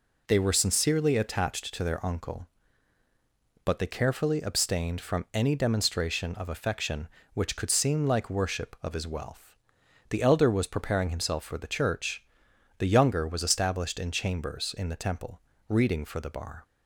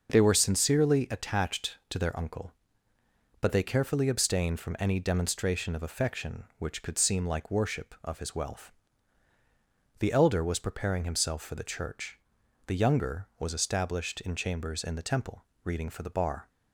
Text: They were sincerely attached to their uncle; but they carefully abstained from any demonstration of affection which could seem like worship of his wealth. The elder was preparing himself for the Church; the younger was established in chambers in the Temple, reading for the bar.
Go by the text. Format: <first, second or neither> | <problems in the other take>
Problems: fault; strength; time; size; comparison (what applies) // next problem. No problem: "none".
neither | none